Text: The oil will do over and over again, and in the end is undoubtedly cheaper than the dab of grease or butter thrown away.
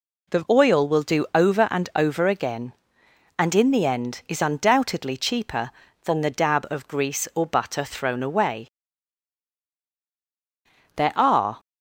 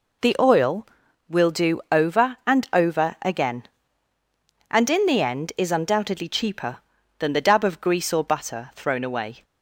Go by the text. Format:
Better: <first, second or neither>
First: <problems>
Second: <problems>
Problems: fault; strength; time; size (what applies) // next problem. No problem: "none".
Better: second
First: goes on to say "There are"; noticeable; from 10.9 s on; 0.64 s long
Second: none